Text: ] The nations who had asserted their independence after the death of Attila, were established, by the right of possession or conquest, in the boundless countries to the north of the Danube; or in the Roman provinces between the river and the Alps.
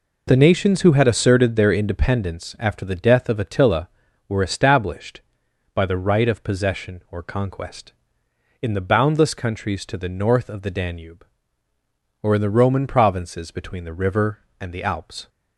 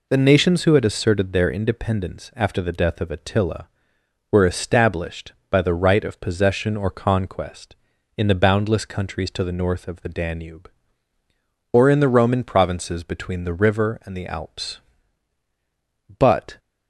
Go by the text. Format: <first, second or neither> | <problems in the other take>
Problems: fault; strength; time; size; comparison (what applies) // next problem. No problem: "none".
first | goes on to say "But"; slight; from 16.1 s on; 0.40 s long